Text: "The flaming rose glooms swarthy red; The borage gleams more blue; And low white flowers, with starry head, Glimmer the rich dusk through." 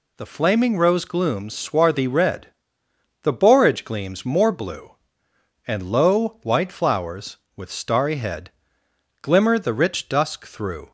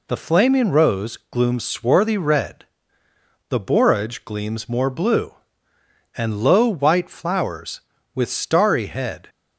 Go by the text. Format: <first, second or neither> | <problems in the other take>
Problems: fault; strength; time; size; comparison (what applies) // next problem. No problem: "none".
first | stops before "Glimmer the rich dusk through"; at 9.2 s